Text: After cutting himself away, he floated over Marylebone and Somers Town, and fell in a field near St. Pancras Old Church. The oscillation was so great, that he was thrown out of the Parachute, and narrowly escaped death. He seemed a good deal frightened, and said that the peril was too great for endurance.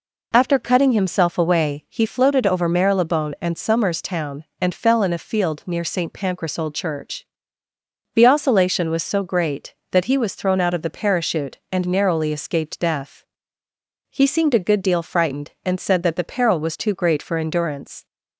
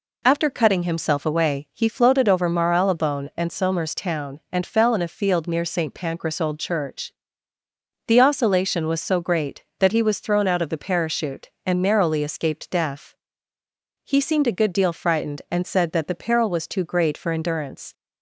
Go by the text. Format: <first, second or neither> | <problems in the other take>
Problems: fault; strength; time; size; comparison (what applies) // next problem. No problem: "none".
neither | none